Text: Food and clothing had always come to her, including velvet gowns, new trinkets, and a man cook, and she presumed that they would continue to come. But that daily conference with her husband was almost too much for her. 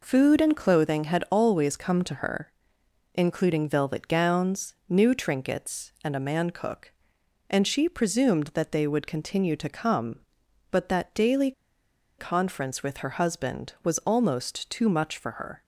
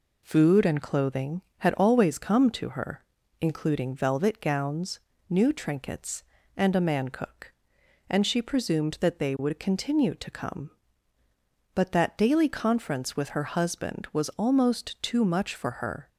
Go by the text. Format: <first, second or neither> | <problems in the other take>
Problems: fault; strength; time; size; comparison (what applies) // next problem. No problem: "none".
second | pauses between "daily" and "conference"; noticeable; at 11.5 s; 0.67 s long